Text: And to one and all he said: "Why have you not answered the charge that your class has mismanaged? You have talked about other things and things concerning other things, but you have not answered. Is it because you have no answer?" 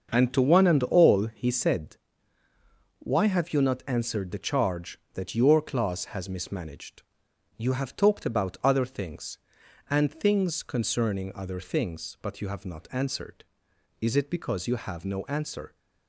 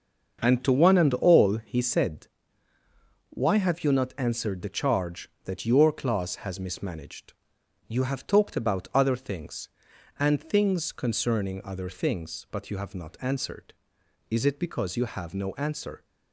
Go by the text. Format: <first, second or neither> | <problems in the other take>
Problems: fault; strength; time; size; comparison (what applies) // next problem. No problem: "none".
neither | starts louder than the rest; the same in both